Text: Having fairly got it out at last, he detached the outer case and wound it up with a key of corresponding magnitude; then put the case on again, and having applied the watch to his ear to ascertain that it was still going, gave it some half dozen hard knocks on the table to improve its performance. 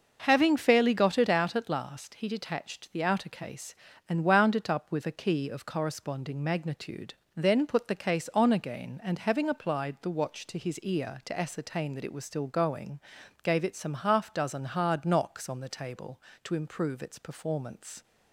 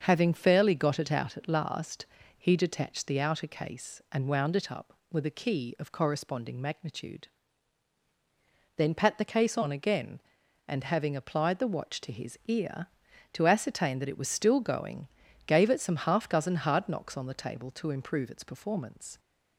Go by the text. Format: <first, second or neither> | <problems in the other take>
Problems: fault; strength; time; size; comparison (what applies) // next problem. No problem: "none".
first | starts louder than the rest; until 1.0 s; 6.5 dB; noticeable in the first // says "pat" for "put"; at 8.9 s